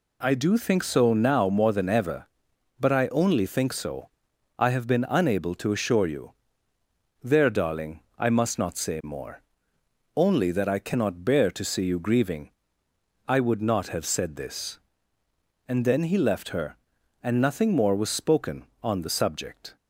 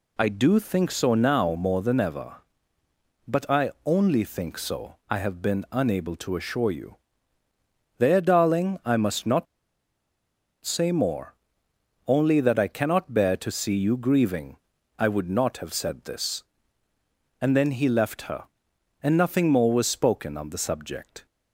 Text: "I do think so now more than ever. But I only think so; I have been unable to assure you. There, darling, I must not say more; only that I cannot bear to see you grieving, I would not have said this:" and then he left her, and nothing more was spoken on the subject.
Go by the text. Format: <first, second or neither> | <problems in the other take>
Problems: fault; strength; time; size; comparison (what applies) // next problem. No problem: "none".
first | pauses between "not" and "say"; at 9.4 s; 1.1 s long